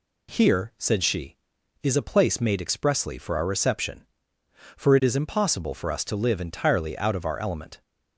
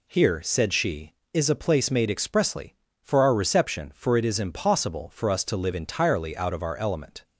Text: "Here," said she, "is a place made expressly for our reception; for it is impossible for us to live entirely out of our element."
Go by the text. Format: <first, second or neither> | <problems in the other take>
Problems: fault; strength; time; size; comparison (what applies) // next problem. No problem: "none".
neither | none